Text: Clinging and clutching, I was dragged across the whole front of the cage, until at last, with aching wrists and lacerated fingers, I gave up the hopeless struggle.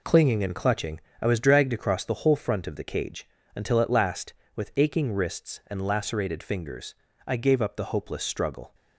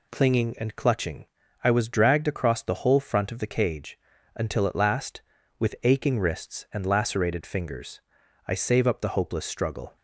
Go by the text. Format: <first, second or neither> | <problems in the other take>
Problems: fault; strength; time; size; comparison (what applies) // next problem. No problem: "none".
first | says "save" for "gave"; at 8.5 s